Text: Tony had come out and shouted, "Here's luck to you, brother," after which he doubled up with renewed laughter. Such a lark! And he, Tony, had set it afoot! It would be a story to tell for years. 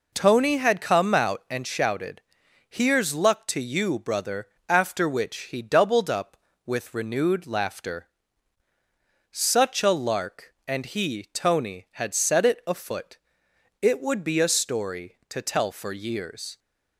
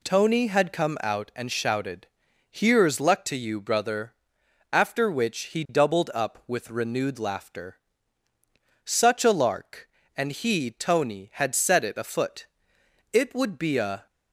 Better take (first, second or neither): first